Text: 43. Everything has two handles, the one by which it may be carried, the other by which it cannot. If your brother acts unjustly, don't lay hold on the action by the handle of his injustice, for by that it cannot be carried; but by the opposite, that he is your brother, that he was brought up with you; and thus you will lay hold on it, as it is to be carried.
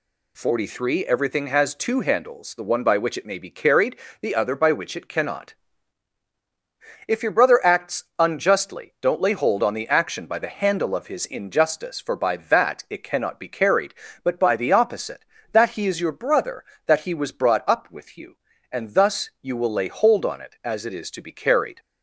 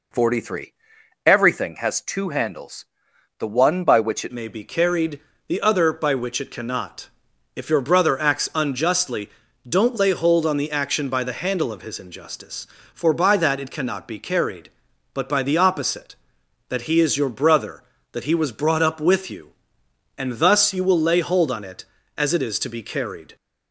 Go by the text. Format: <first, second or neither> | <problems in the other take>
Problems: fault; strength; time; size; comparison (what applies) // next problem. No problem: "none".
first | changes voice at "may"; from 4.3 s on; 19.0 s long